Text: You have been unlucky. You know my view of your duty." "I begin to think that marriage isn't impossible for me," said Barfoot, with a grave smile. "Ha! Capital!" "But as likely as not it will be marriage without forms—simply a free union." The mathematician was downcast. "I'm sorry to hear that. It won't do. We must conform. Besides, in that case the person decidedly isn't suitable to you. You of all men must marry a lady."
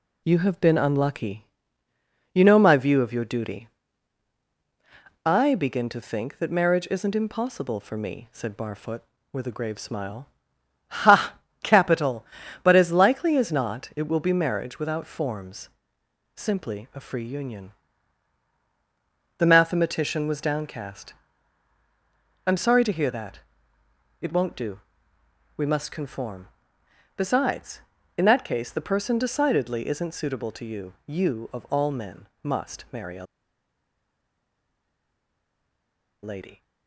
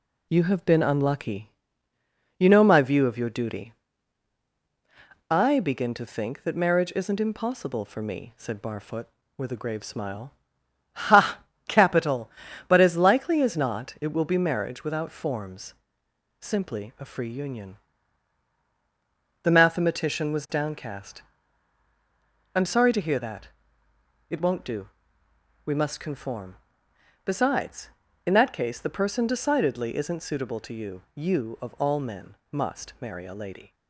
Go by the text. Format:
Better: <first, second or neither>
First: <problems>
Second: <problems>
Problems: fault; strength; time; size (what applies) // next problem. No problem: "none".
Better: second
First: pauses between "men" and "must"; slight; at 32.2 s; 0.16 s long // pauses between "a" and "lady"; strong; at 33.2 s; 2.9 s long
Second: pauses between "men" and "must"; slight; at 32.3 s; 0.16 s long